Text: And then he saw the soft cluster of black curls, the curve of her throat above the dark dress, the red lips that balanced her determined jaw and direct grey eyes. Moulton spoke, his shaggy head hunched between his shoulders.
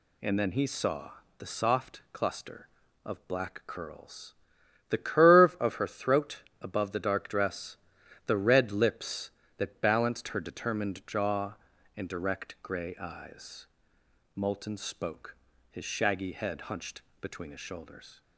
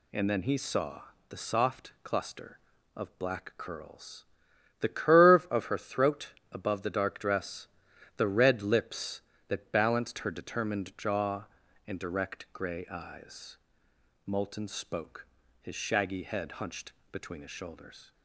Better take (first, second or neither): neither